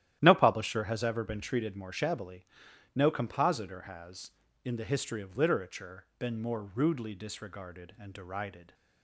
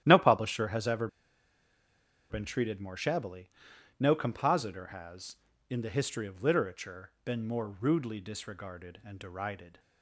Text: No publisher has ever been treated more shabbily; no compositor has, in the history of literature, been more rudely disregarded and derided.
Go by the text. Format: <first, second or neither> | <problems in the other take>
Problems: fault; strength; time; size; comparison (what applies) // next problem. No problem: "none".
first | starts louder than the rest; strong; until 1.0 s; 12 dB; strong in the first // pauses between "ever" and "been"; at 1.0 s; 1.2 s long